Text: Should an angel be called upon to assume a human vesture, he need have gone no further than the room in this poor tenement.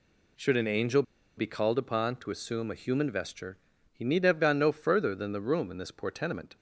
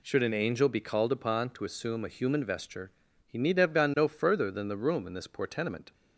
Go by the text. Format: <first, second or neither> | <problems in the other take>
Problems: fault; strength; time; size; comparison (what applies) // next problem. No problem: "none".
second | pauses between "angel" and "be"; slight; at 1.0 s; 0.35 s long